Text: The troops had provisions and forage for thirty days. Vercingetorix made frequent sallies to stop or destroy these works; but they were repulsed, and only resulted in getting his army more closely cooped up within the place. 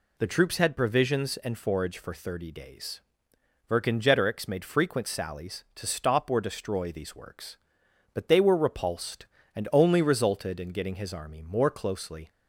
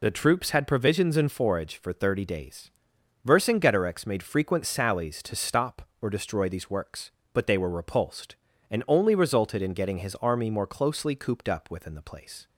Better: second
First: stops before "cooped up within the place"; at 12.2 s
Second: none

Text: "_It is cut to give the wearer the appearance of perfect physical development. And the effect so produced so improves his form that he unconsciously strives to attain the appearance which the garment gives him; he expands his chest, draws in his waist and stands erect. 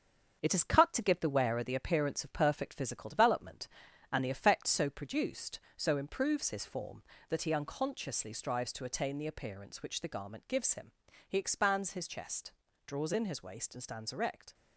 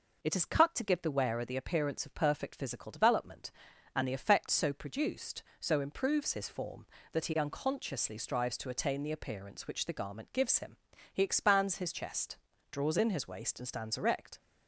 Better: second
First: gets quieter; noticeable; throughout; 5.5 dB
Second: none

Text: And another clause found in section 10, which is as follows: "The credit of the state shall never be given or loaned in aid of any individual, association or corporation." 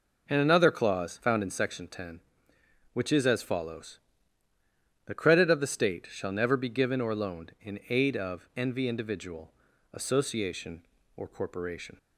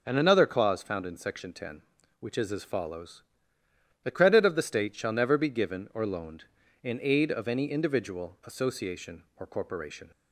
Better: second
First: says "envy" for "any"; at 8.5 s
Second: none

